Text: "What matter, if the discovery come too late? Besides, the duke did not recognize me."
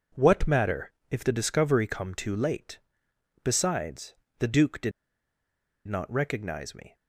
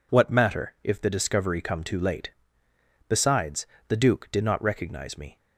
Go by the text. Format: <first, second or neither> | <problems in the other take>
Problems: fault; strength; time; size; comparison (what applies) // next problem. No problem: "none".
second | pauses between "did" and "not"; noticeable; at 4.9 s; 0.96 s long